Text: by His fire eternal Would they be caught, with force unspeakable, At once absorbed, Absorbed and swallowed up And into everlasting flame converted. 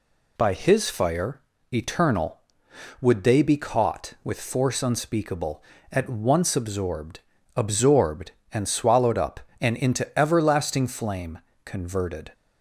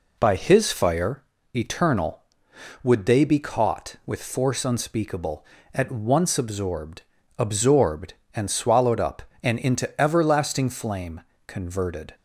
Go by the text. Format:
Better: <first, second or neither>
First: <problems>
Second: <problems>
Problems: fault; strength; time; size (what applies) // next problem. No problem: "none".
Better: first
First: pauses between "fire" and "eternal"; slight; at 1.3 s; 0.34 s long // pauses between "flame" and "converted"; slight; at 11.3 s; 0.24 s long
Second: starts louder than the rest; slight; until 1.2 s; 3.5 dB // pauses between "fire" and "eternal"; slight; at 1.2 s; 0.34 s long // pauses between "flame" and "converted"; slight; at 11.2 s; 0.24 s long